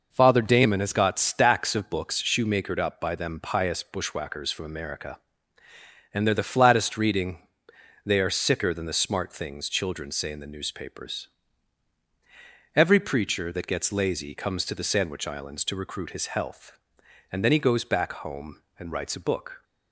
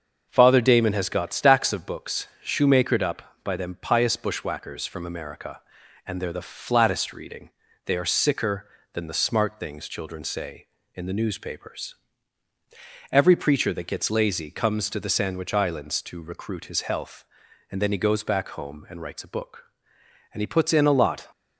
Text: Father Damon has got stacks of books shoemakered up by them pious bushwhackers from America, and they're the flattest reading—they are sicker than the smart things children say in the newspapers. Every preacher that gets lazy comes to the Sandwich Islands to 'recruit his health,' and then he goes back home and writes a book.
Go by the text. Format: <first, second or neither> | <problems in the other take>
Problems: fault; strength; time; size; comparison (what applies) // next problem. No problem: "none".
first | starts louder than the rest; until 1.3 s; 6.5 dB // pauses between "books" and "shoemakered"; slight; at 2.2 s; 0.16 s long // goes on to say "And he puts in a lot"; noticeable; from 20.3 s on; 0.94 s long